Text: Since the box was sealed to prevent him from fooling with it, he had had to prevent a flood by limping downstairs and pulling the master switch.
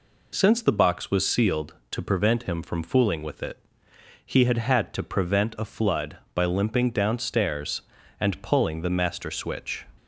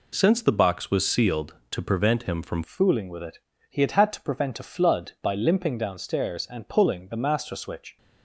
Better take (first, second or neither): first